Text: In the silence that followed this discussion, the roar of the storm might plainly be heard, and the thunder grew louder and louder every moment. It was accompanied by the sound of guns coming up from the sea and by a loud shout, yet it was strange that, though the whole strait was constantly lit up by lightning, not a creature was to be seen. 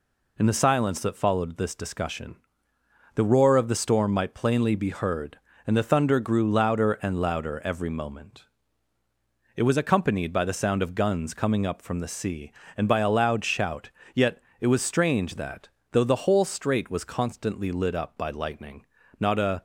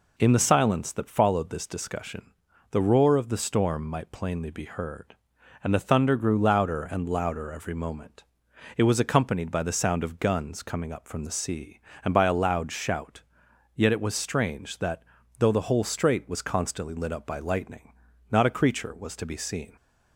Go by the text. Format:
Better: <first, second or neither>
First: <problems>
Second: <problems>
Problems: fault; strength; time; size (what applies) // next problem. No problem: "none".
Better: second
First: pauses between "yet" and "it"; slight; at 14.4 s; 0.18 s long // stops before "creature was to be seen"; at 19.5 s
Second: none